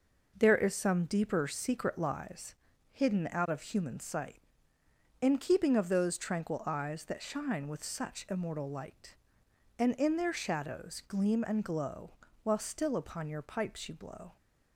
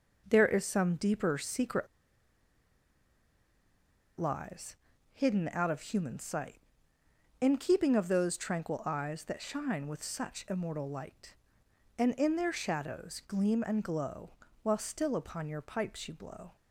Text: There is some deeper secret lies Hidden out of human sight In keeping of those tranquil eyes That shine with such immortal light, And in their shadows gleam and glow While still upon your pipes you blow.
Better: first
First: pauses between "lies" and "Hidden"; slight; at 2.5 s; 0.34 s long // pauses between "glow" and "While"; slight; at 12.1 s; 0.32 s long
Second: pauses between "secret" and "lies"; strong; at 1.8 s; 2.3 s long // pauses between "lies" and "Hidden"; slight; at 4.7 s; 0.34 s long // pauses between "glow" and "While"; slight; at 14.3 s; 0.32 s long

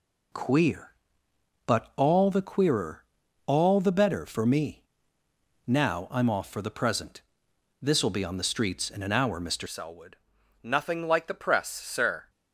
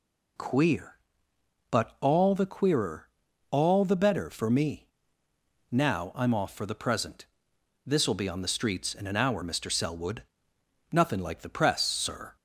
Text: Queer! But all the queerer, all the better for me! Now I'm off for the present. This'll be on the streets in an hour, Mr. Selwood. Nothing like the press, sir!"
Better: second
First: changes voice at "Selwood"; from 9.6 s on; 2.6 s long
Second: none

